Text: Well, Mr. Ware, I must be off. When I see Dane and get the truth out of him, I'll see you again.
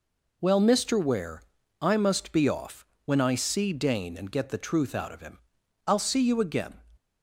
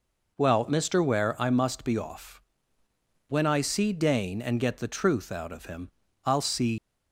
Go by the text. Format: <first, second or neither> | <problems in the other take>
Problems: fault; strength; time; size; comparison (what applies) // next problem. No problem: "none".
first | stops before "you again"; at 6.7 s